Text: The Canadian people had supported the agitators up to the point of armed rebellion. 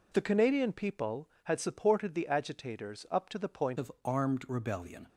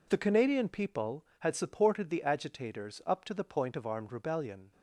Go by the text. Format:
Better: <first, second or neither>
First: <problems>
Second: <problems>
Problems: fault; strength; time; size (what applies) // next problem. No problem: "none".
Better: second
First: changes voice at "of"; from 3.7 s on; 1.3 s long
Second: none